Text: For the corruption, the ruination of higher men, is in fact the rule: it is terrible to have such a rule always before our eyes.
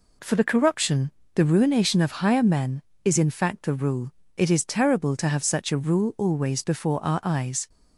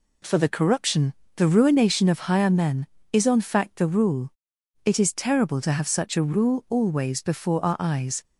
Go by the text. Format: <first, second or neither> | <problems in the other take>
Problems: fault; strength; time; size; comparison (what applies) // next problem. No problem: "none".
first | says "on" for "in"; at 3.2 s